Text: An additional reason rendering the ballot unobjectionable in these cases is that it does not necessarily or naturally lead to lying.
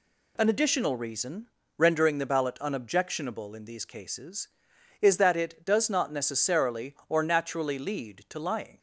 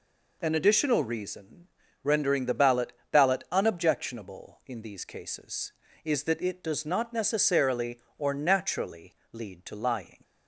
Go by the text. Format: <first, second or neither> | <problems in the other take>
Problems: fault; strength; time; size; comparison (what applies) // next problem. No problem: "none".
first | pauses between "reason" and "rendering"; at 1.6 s; 0.38 s long; slight in the first // says "ballot" twice; at 3.1 s // pauses between "naturally" and "lead"; slight; at 9.1 s; 0.18 s long